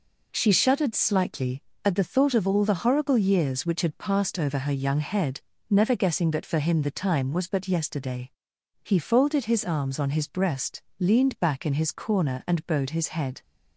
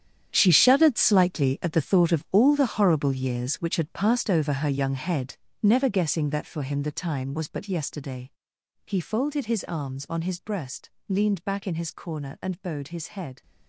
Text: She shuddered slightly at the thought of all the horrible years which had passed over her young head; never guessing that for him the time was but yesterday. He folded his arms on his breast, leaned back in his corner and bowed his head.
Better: first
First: none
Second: gets quieter; strong; throughout; 14 dB

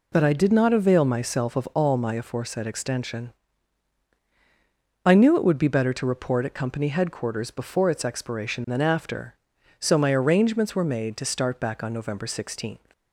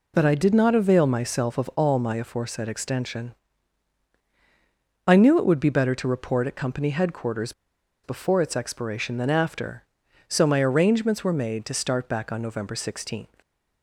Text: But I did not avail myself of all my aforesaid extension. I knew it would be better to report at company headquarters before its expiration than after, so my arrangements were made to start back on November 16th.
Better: first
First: none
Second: pauses between "headquarters" and "before"; noticeable; at 7.5 s; 0.52 s long

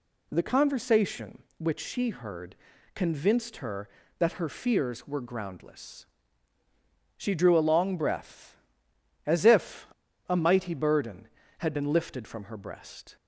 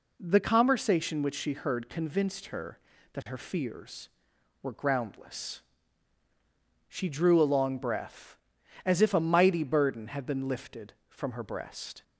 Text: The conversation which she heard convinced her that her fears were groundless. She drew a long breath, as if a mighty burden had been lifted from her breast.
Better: second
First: pauses between "heard" and "convinced"; at 2.5 s; 0.40 s long // pauses between "if" and "a"; at 9.8 s; 0.41 s long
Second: none

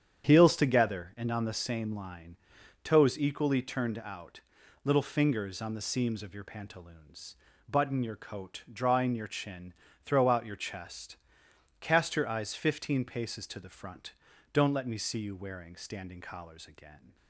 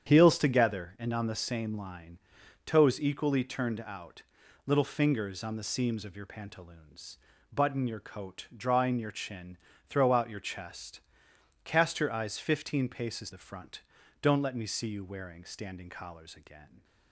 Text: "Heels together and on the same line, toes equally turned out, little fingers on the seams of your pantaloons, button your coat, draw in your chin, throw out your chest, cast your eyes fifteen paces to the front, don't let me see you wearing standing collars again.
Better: first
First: starts louder than the rest; strong; until 1.2 s; 8.5 dB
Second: starts louder than the rest; strong; until 1.1 s; 8.5 dB // skips "to"; at 13.3 s

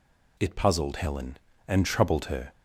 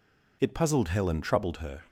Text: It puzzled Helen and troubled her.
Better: first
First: none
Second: skips "and"; at 1.2 s

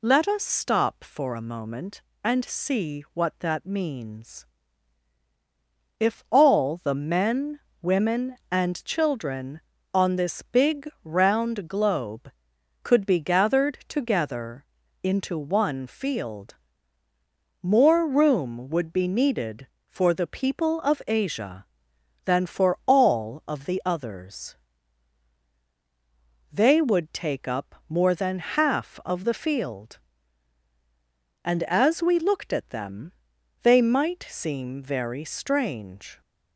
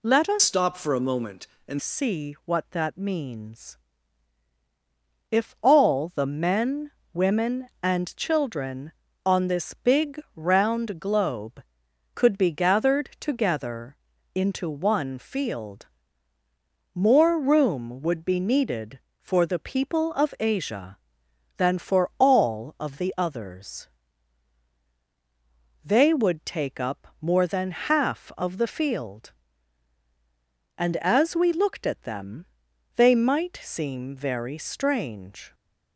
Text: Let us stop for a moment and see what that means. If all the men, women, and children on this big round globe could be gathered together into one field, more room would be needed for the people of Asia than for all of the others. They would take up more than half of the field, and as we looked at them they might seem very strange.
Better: first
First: pauses between "big" and "round"; slight; at 10.8 s; 0.16 s long // pauses between "together" and "into"; slight; at 14.6 s; 0.36 s long // pauses between "them" and "they"; noticeable; at 33.1 s; 0.52 s long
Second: changes voice from "stop" to "and"; from 0.3 to 1.7 s; 1.4 s long // pauses between "big" and "round"; slight; at 10.1 s; 0.16 s long // pauses between "together" and "into"; slight; at 13.9 s; 0.36 s long // pauses between "them" and "they"; noticeable; at 32.4 s; 0.52 s long

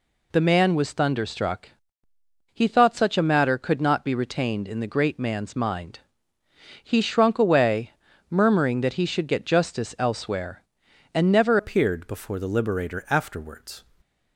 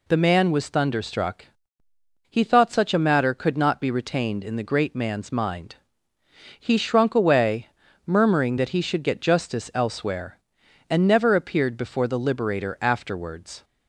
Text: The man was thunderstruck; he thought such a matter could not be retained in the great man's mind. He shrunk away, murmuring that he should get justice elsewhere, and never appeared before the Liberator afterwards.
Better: second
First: changes voice at "appeared"; from 11.5 s on; 2.3 s long // stays silent after the last word; slight; from 13.8 s on; 0.5 s long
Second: none

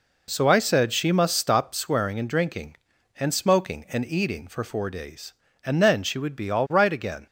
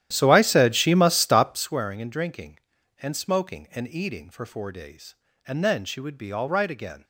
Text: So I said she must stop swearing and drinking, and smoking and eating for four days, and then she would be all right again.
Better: first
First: none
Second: starts louder than the rest; strong; until 1.8 s; 11.5 dB

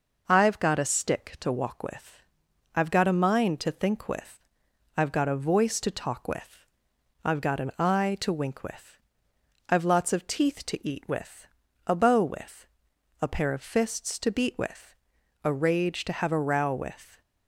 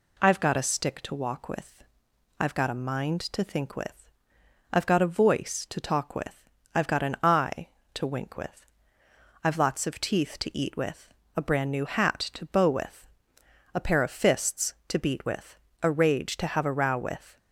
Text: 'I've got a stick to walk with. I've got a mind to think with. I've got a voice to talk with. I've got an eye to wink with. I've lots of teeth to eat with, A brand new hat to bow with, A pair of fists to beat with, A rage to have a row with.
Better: second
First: skips "brand new hat to"; at 11.9 s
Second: none

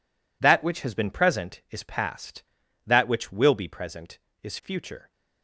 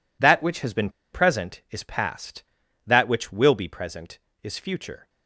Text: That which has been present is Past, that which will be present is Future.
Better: first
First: none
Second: pauses between "been" and "present"; slight; at 0.9 s; 0.22 s long

